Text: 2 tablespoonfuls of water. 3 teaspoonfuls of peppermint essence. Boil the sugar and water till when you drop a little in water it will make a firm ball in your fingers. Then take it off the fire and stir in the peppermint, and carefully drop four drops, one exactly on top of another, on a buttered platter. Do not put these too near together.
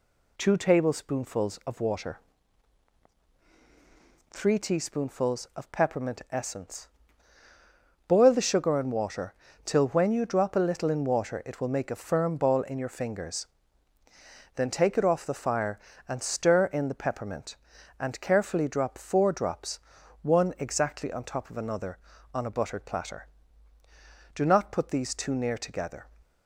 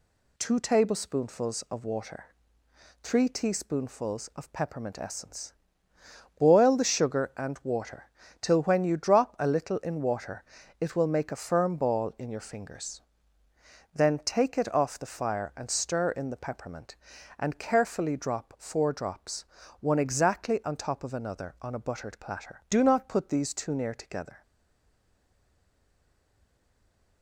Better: first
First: pauses between "water" and "till"; slight; at 9.3 s; 0.30 s long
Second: pauses between "water" and "till"; slight; at 8.0 s; 0.32 s long // pauses between "water" and "it"; slight; at 10.4 s; 0.36 s long // stays silent after the last word; strong; from 24.4 s on; 2.8 s long

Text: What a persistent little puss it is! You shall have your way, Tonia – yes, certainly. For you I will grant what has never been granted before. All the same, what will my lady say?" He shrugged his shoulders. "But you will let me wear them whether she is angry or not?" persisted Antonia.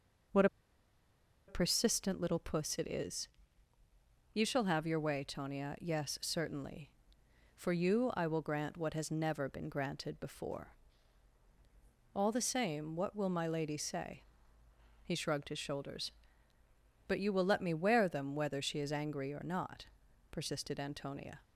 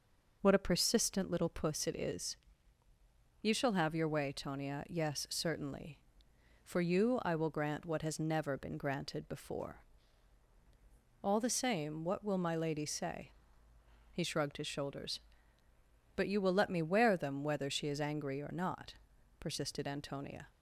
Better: second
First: pauses between "What" and "a"; at 0.4 s; 1.0 s long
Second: none

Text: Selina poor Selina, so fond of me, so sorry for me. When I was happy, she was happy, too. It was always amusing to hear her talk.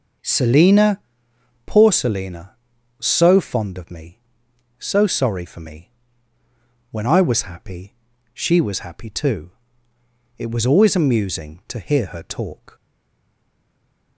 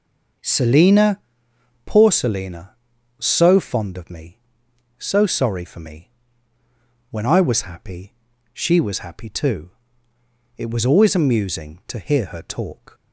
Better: second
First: pauses between "Selina" and "poor"; noticeable; at 0.9 s; 0.66 s long // stays silent after the last word; noticeable; from 12.7 s on; 1.4 s long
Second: pauses between "Selina" and "poor"; noticeable; at 1.1 s; 0.66 s long

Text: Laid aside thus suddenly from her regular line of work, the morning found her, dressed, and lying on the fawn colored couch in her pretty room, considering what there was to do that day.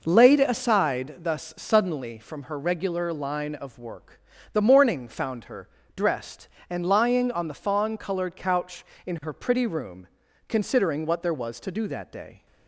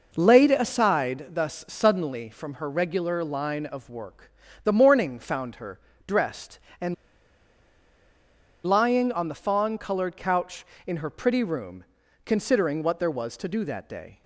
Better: first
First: none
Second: pauses between "and" and "lying"; strong; at 6.9 s; 1.6 s long

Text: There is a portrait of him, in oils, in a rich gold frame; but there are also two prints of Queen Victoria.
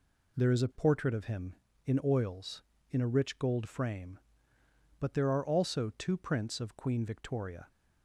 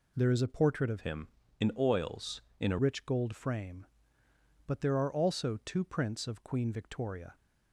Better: first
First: none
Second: changes voice from "him" to "a"; from 1.0 to 2.7 s; 1.7 s long

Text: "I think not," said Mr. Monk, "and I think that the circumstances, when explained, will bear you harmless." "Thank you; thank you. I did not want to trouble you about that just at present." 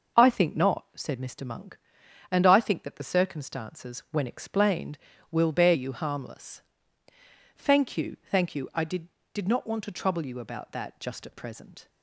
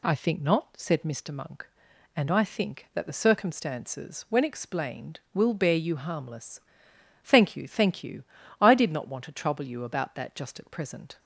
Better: second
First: says "did" twice; at 9.3 s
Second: none

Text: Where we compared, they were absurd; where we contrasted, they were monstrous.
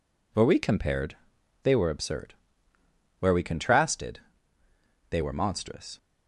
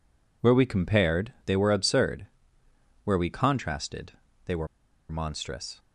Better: first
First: none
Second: pauses between "were" and "monstrous"; at 4.6 s; 0.43 s long

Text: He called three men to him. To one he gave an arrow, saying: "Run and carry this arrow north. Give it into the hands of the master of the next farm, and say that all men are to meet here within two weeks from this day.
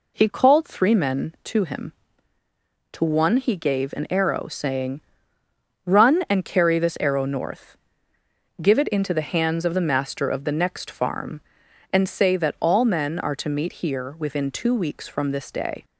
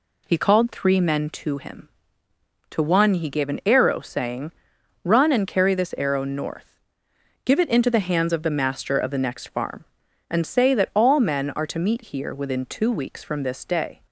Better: neither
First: none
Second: none

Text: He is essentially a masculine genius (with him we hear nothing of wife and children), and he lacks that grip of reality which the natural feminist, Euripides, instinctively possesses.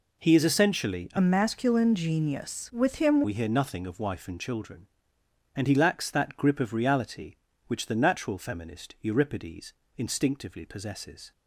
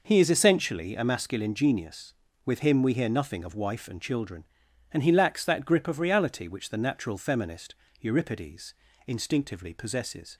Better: second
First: changes voice from "masculine" to "him"; from 1.1 to 3.2 s; 2.1 s long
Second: none

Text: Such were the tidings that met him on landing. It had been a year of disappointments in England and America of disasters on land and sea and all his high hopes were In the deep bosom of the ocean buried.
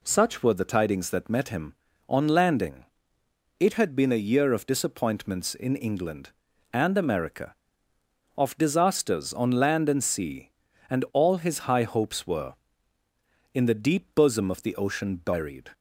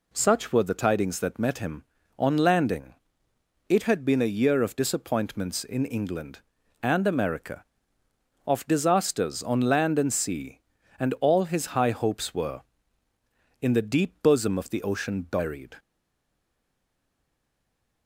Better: first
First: none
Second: stays silent after the last word; from 15.7 s on; 2.3 s long

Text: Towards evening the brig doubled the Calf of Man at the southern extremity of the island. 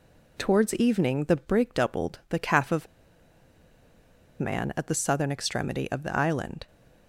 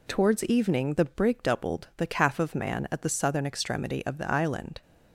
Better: second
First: pauses between "of" and "Man"; strong; at 2.8 s; 1.5 s long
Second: none

